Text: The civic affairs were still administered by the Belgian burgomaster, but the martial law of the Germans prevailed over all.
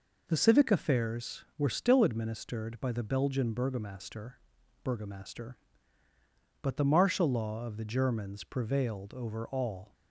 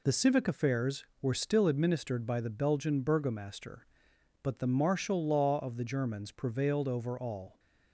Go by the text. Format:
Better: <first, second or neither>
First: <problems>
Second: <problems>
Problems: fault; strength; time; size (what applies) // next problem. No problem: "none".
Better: second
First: says "burgomaster" twice; at 4.8 s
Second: none